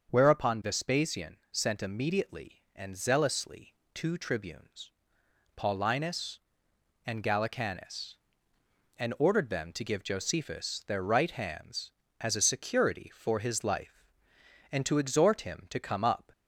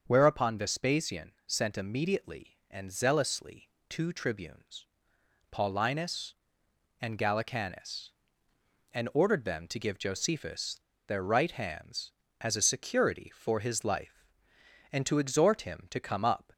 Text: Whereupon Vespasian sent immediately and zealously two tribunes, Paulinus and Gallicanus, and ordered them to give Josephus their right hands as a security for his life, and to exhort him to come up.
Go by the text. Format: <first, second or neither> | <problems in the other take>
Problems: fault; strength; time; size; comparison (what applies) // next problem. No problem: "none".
first | starts louder than the rest; until 1.0 s; 6.5 dB; also in the first // pauses between "zealously" and "two"; slight; at 3.6 s; 0.20 s long; slight in the first // pauses between "Josephus" and "their"; slight; at 10.7 s; 0.29 s long